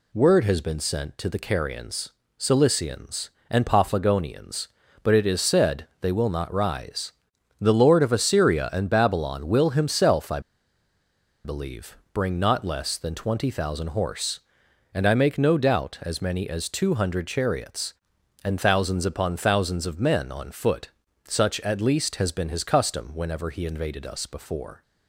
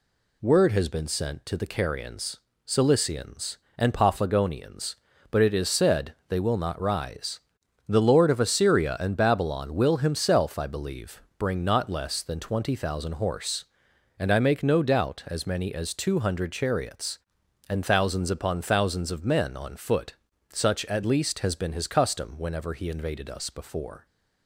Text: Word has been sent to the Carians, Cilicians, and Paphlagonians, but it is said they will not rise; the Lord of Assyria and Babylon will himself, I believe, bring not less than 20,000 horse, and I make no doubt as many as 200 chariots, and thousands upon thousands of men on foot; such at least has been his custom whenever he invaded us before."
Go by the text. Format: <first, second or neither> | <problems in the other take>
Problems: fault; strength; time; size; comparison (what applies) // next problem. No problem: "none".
second | pauses between "I" and "believe"; at 10.3 s; 1.0 s long